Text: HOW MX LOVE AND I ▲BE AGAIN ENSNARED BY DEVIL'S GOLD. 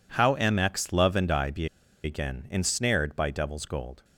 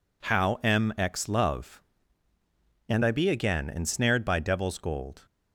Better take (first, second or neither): second